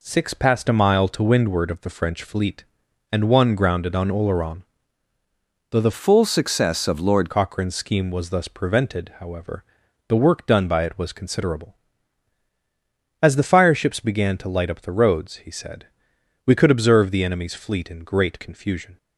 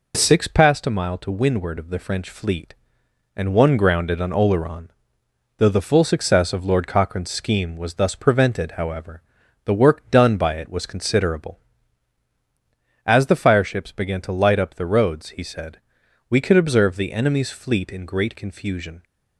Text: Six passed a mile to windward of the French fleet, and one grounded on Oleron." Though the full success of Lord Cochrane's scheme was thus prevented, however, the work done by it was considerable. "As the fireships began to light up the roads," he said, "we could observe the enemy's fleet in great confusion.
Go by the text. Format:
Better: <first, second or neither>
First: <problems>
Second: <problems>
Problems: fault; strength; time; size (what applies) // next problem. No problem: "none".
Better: second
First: changes voice from "full" to "Lord"; from 5.9 to 7.3 s; 1.4 s long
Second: none